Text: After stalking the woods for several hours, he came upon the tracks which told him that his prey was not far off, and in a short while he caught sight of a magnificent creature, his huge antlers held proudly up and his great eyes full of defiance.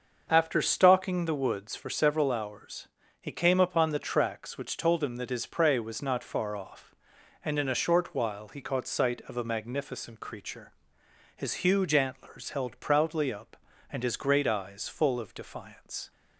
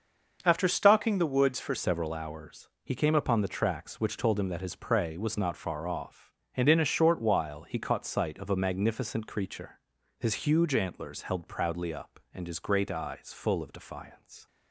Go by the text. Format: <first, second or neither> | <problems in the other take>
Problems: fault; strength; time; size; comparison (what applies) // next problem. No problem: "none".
first | starts louder than the rest; until 1.4 s; 6 dB; also in the first // changes voice at "several"; from 1.7 s on; 12.7 s long